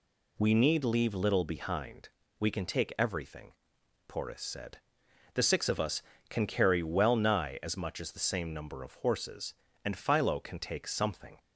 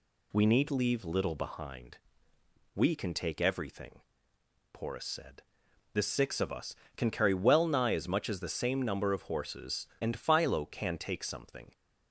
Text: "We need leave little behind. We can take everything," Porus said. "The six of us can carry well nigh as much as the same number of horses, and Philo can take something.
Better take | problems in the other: neither | none

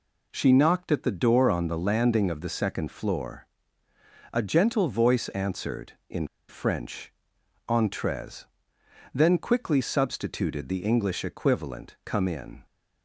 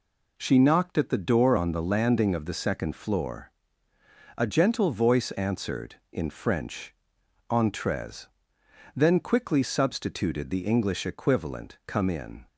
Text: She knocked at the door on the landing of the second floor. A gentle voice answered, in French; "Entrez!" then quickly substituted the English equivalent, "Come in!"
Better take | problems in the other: second | pauses between "in" and "French"; slight; at 6.2 s; 0.21 s long

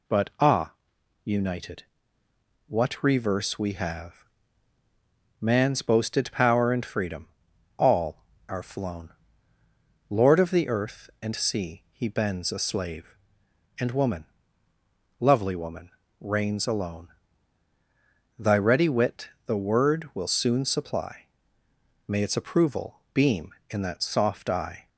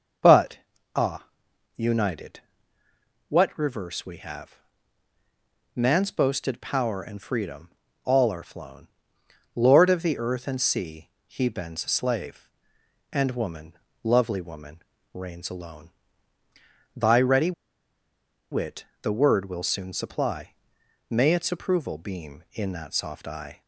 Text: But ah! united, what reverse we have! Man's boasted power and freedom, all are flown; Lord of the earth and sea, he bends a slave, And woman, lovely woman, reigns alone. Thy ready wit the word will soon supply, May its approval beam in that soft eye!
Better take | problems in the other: first | starts louder than the rest; until 2.1 s; 6 dB // pauses between "But" and "ah"; at 0.5 s; 0.38 s long // pauses between "ready" and "wit"; at 17.5 s; 0.99 s long // pauses between "wit" and "the"; slight; at 18.8 s; 0.18 s long; slight in the first

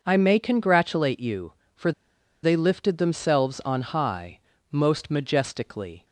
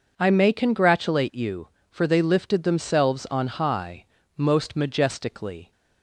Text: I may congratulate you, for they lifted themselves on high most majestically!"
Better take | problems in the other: second | pauses between "for" and "they"; noticeable; at 1.9 s; 0.51 s long // pauses between "high" and "most"; slight; at 4.3 s; 0.30 s long; slight in the second

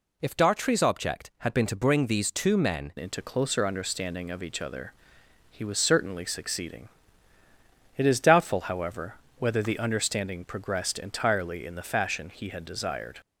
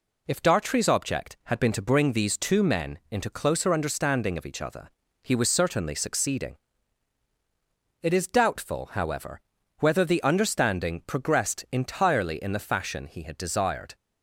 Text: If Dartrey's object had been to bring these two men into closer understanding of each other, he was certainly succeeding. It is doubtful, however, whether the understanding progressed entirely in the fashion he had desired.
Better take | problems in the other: second | changes voice at "into"; from 2.9 s on; 10.3 s long

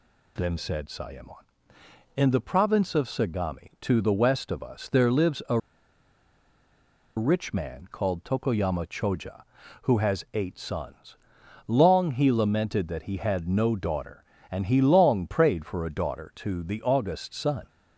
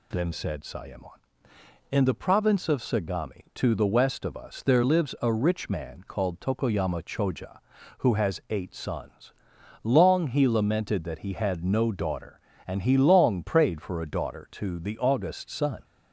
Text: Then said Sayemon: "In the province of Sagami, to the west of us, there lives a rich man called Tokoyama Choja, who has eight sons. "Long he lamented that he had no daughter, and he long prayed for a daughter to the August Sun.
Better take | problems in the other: second | pauses between "a" and "rich"; strong; at 5.5 s; 1.5 s long

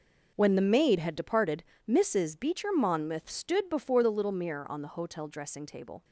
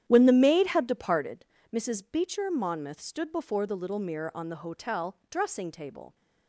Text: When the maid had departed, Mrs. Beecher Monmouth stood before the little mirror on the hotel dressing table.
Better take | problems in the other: first | starts louder than the rest; strong; until 1.5 s; 10.5 dB

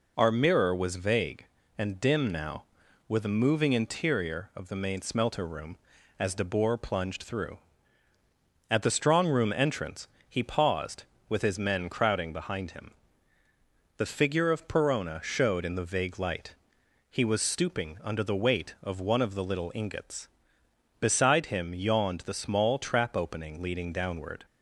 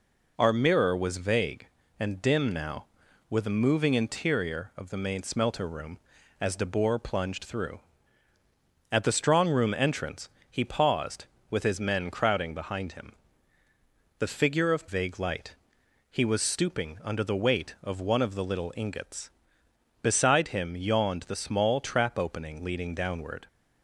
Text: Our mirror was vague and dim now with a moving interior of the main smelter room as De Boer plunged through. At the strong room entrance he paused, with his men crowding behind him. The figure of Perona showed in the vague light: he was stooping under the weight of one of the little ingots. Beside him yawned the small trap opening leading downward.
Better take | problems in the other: first | pauses between "entrance" and "he"; slight; at 10.2 s; 0.22 s long; slight in the first // skips "Perona showed in the"; at 14.8 s

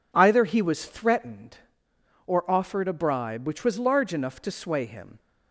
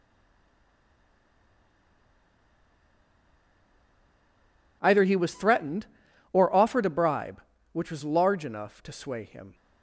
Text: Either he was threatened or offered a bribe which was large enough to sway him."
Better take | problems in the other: first | stays silent before the first word; strong; until 4.8 s; 4.8 s long

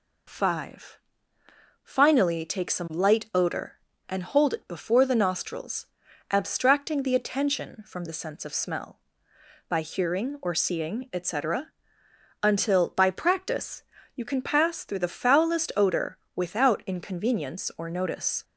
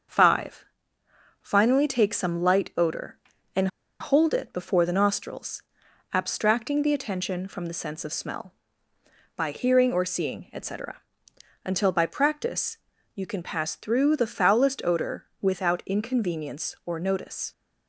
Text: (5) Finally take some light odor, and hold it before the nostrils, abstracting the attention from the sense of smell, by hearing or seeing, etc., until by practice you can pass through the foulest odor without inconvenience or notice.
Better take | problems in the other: first | starts louder than the rest; until 1.8 s; 6.5 dB // pauses between "and" and "hold"; slight; at 3.6 s; 0.32 s long // pauses between "practice" and "you"; slight; at 12.7 s; 0.36 s long; slight in the first // pauses between "odor" and "without"; slight; at 15.2 s; 0.16 s long; slight in the first

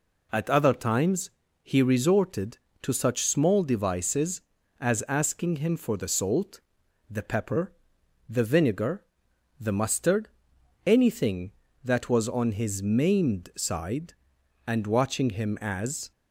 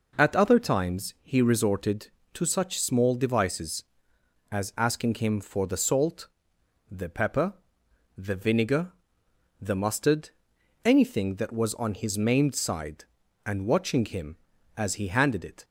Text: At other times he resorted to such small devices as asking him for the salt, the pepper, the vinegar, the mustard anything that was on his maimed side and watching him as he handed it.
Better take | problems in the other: second | pauses between "times" and "he"; slight; at 1.2 s; 0.34 s long // pauses between "mustard" and "anything"; noticeable; at 10.2 s; 0.56 s long; noticeable in the second // stops before "he handed it"; at 16.1 s

